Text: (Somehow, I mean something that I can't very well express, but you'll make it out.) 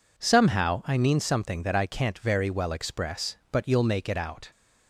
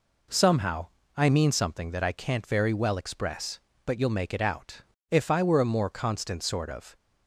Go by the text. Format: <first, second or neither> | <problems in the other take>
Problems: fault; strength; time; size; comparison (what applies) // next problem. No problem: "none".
first | goes on to say "If I were a more constant sort of"; strong; from 5.0 s on; 1.8 s long